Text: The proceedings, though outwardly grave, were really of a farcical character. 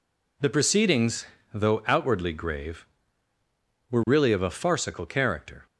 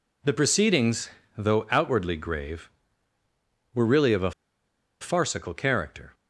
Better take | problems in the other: first | pauses between "a" and "farcical"; noticeable; at 4.3 s; 0.70 s long

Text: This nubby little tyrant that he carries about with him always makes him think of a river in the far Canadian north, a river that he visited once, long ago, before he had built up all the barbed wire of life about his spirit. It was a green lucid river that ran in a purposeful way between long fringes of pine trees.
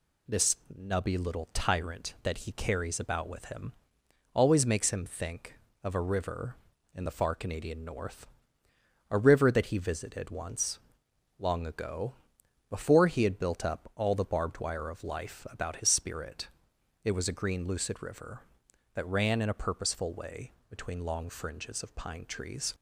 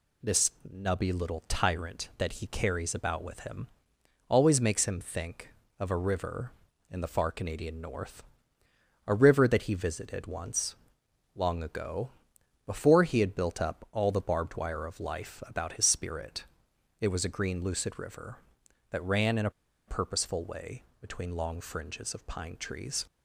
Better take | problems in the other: first | pauses between "This" and "nubby"; slight; at 0.5 s; 0.20 s long; slight in the first // pauses between "him" and "always"; noticeable; at 3.6 s; 0.62 s long; noticeable in the first // pauses between "a" and "purposeful"; at 19.4 s; 0.37 s long // pauses between "way" and "between"; slight; at 20.8 s; 0.18 s long; slight in the first

